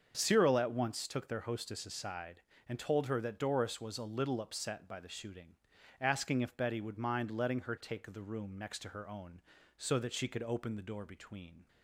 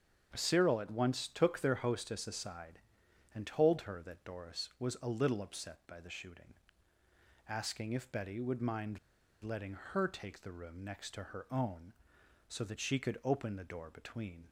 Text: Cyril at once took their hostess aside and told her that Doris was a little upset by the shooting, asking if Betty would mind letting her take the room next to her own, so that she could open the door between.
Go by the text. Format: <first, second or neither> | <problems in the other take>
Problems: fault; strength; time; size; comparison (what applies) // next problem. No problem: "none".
first | starts louder than the rest; strong; until 1.3 s; 7.5 dB; also in the first // pauses between "mind" and "letting"; at 8.9 s; 0.44 s long